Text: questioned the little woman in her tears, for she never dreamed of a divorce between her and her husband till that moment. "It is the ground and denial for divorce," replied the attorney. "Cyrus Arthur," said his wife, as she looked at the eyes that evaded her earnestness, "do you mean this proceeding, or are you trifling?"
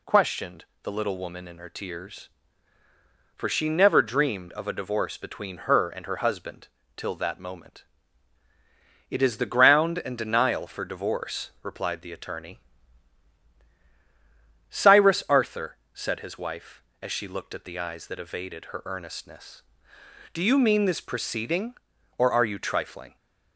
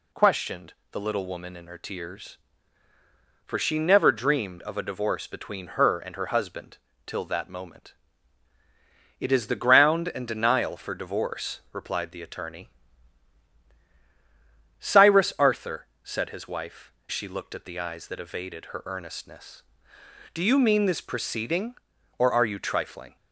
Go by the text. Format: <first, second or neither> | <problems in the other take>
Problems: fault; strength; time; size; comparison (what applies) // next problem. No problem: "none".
first | pauses between "questioned" and "the"; slight; at 0.7 s; 0.18 s long; slight in the first // pauses between "husband" and "till"; slight; at 6.7 s; 0.28 s long; slight in the first // skips "as"; at 17.0 s